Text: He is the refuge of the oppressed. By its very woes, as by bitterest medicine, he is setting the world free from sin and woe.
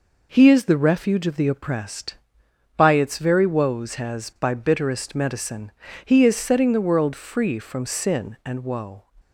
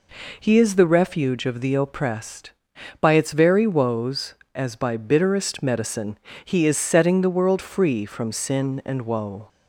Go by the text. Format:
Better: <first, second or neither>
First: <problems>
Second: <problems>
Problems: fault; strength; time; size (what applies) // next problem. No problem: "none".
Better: second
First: says "has" for "as"; at 3.9 s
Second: none